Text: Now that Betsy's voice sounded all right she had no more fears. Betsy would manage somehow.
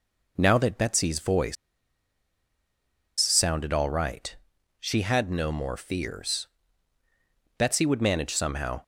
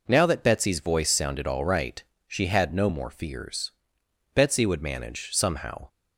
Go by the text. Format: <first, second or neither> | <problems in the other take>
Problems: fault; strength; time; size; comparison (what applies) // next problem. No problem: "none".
second | pauses between "voice" and "sounded"; strong; at 1.5 s; 1.6 s long // pauses between "right" and "she"; noticeable; at 4.3 s; 0.46 s long; slight in the second